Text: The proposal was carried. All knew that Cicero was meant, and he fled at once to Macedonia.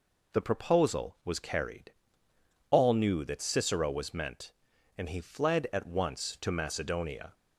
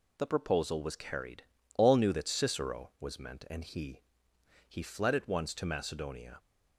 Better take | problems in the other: first | says "he" twice; at 4.6 s

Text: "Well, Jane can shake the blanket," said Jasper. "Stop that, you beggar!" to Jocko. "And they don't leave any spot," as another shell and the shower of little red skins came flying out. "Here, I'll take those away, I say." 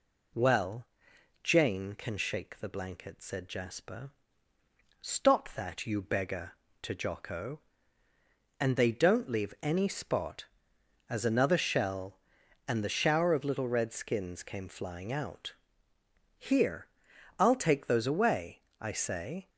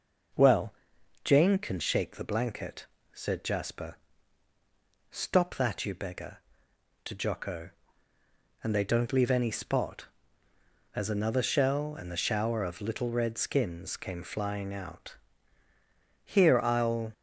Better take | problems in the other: first | stops before "take those away I say"; at 17.1 s

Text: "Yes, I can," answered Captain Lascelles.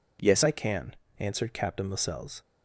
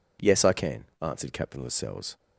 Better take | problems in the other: second | changes voice at "I"; from 0.4 s on; 2.0 s long

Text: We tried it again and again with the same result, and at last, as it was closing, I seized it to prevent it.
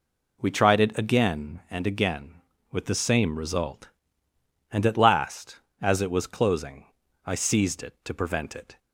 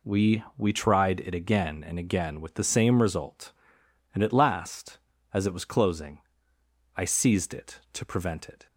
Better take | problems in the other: first | says "We" twice; at 0.5 s

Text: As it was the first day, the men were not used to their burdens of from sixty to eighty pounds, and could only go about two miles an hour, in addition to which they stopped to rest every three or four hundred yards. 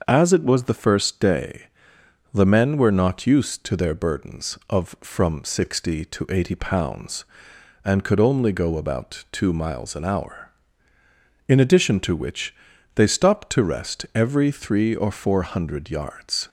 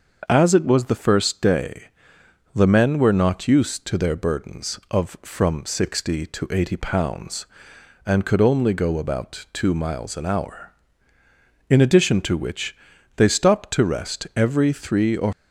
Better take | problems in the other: first | starts louder than the rest; until 1.3 s; 6.5 dB; also in the first // pauses between "which" and "they"; at 12.7 s; 0.40 s long; also in the first // stops before "four hundred yards"; at 15.3 s

